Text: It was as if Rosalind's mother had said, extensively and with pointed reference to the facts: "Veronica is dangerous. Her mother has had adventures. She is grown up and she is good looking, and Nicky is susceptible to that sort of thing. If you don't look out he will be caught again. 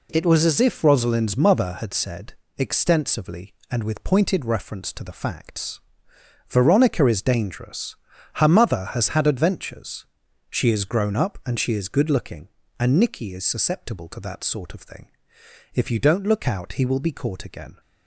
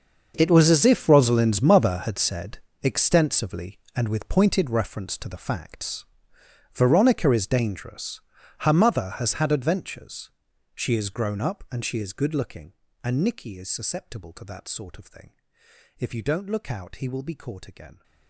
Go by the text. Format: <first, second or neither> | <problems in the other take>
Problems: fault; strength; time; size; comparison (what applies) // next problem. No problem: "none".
first | gets quieter; strong; throughout; 17 dB